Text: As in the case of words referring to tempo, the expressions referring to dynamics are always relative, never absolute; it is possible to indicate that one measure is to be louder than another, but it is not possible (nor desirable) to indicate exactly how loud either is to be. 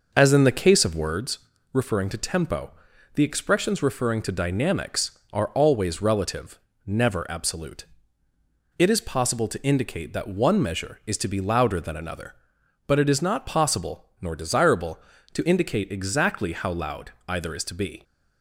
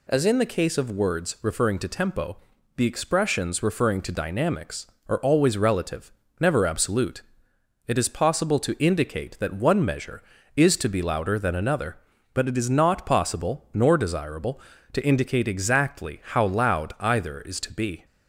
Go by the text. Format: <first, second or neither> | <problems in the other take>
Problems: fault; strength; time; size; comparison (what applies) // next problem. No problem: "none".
second | starts louder than the rest; noticeable; until 1.2 s; 6 dB // pauses between "words" and "referring"; slight; at 1.3 s; 0.34 s long // pauses between "loud" and "either"; slight; at 17.1 s; 0.18 s long